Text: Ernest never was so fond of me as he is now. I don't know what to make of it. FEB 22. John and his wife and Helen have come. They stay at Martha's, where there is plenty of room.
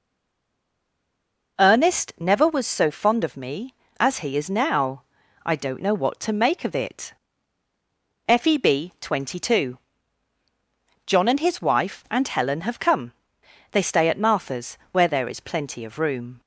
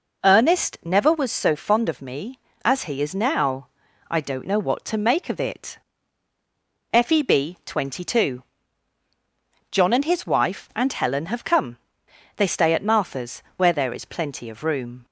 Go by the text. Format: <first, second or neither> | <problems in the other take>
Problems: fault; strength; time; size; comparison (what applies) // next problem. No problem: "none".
second | stays silent before the first word; noticeable; until 1.5 s; 1.5 s long